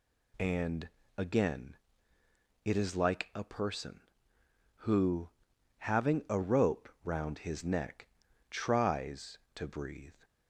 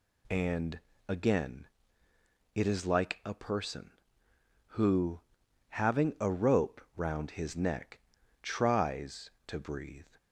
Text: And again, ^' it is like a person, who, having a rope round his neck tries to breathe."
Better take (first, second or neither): neither